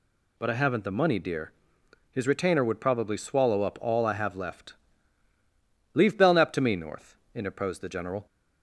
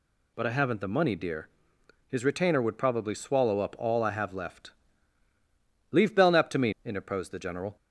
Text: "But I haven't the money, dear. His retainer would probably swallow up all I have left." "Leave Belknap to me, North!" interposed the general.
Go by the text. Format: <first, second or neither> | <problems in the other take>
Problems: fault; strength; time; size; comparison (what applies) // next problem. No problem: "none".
first | skips "North"; at 6.7 s